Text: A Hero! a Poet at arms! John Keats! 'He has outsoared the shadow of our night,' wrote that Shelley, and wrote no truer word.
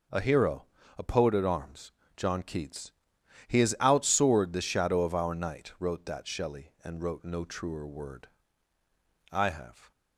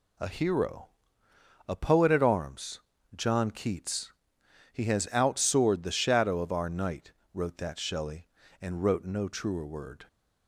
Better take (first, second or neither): second